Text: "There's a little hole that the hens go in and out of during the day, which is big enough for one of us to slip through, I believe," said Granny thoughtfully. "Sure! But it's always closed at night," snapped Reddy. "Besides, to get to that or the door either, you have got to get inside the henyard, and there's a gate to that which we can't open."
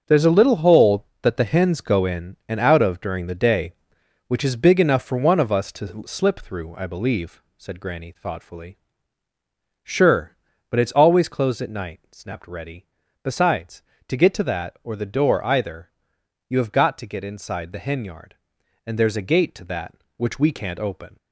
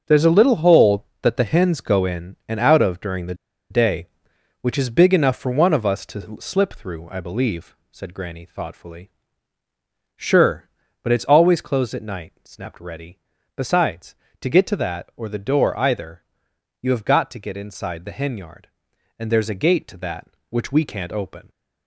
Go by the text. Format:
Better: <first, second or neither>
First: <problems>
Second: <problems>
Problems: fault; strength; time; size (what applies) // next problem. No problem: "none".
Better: first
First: starts louder than the rest; until 1.0 s; 6.5 dB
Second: starts louder than the rest; until 1.0 s; 6.5 dB // pauses between "the" and "day"; at 3.3 s; 0.36 s long